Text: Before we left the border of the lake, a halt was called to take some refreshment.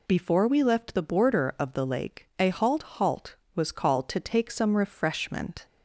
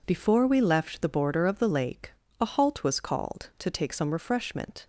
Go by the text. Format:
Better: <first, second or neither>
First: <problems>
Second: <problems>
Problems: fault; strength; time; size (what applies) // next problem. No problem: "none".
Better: second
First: says "halt" twice; at 2.8 s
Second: none